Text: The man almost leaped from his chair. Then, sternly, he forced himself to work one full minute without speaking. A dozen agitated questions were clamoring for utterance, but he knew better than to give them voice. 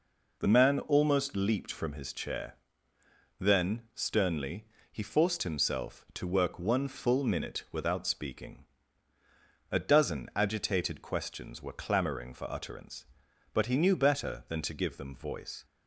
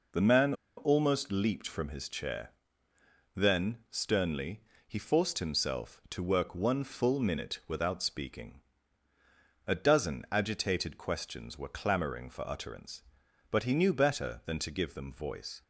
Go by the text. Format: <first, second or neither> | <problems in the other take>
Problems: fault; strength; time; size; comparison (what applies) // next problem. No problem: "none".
first | pauses between "man" and "almost"; slight; at 0.5 s; 0.23 s long